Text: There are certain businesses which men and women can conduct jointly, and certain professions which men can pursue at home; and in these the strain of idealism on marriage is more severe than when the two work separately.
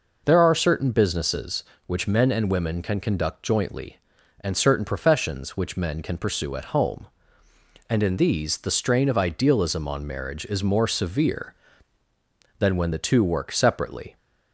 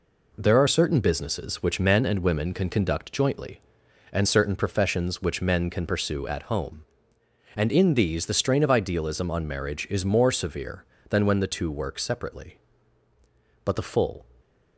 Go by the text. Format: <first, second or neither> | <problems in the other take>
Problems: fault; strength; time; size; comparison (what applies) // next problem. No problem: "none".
first | goes on to say "But the full"; noticeable; from 13.6 s on; 0.64 s long